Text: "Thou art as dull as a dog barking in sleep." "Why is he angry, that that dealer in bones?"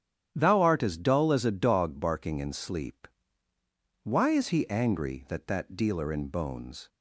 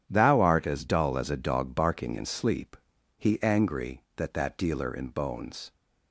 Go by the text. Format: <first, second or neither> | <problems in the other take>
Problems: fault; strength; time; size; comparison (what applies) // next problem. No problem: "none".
first | starts louder than the rest; strong; until 1.0 s; 10 dB; strong in the first // skips "Why is"; at 2.9 s